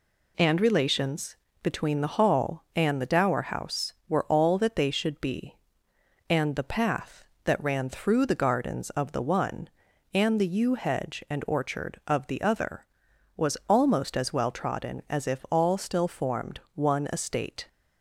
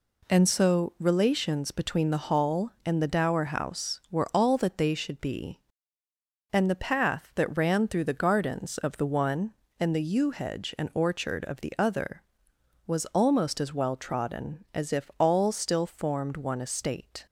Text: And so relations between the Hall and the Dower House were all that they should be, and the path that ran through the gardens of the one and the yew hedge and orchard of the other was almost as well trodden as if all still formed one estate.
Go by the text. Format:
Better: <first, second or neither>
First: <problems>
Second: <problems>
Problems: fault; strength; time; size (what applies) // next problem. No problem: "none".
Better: second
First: skips "so"; at 0.5 s // pauses between "relations" and "between"; slight; at 1.3 s; 0.26 s long // pauses between "formed" and "one"; slight; at 16.5 s; 0.16 s long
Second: none